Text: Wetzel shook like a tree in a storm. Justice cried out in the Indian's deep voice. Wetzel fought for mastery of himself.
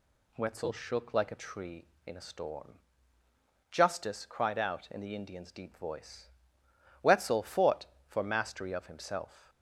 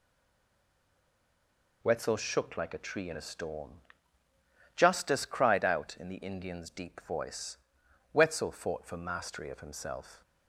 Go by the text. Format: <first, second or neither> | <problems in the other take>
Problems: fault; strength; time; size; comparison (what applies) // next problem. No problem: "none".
first | stays silent before the first word; noticeable; until 1.8 s; 1.8 s long